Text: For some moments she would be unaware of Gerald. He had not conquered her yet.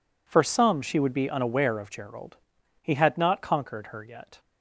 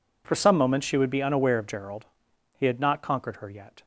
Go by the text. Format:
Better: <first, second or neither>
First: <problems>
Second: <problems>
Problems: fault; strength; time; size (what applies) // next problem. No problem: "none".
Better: second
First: skips "moments"; at 0.8 s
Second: none